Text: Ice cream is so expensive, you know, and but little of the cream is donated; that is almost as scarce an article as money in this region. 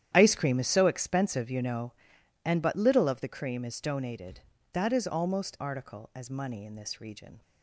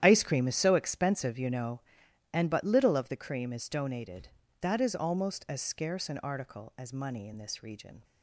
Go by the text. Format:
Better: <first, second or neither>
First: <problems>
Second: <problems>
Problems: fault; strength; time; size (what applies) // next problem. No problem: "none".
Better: second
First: starts louder than the rest; strong; until 1.1 s; 10.5 dB // skips "as scarce an"; at 5.5 s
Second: starts louder than the rest; strong; until 1.0 s; 10.5 dB